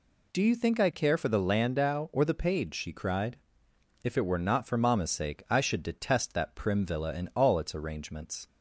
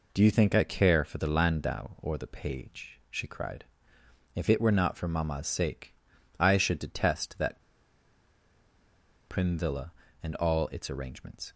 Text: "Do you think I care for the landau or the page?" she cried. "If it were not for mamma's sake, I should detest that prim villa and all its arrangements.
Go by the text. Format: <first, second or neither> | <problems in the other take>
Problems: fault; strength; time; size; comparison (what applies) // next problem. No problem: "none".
first | pauses between "that" and "prim"; strong; at 7.6 s; 1.6 s long